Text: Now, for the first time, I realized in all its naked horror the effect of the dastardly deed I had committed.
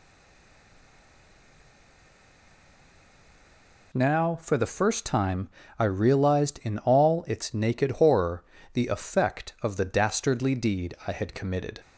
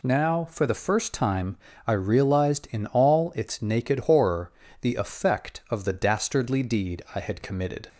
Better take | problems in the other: second | stays silent before the first word; strong; until 3.9 s; 3.9 s long // pauses between "horror" and "the"; slight; at 8.4 s; 0.30 s long; slight in the second

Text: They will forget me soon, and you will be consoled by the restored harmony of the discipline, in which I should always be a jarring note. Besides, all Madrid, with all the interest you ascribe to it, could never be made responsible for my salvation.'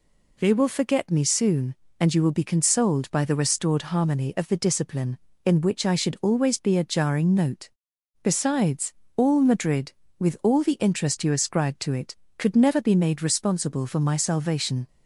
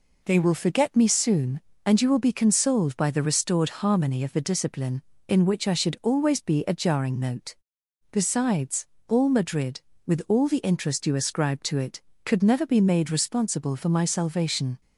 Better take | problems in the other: neither | none

